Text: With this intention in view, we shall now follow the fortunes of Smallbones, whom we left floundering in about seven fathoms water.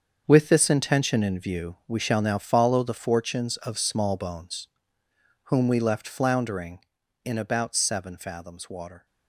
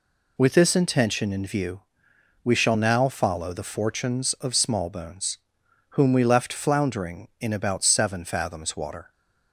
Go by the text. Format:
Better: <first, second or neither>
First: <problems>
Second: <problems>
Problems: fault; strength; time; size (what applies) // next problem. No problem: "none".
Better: second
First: gets quieter; strong; throughout; 11.5 dB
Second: none